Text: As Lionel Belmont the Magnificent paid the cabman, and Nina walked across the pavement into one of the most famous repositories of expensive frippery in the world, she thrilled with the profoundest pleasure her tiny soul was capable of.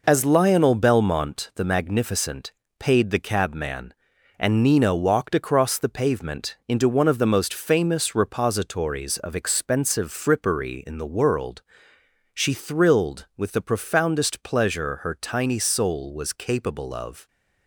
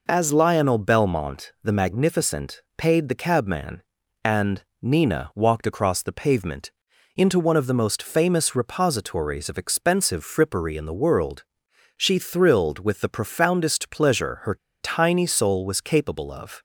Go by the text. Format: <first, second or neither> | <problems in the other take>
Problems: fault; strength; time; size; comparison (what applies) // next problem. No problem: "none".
first | pauses between "Magnificent" and "paid"; slight; at 2.6 s; 0.16 s long; slight in the first // pauses between "and" and "Nina"; slight; at 4.6 s; 0.18 s long // pauses between "pavement" and "into"; noticeable; at 6.6 s; 0.46 s long // pauses between "her" and "tiny"; slight; at 14.5 s; 0.24 s long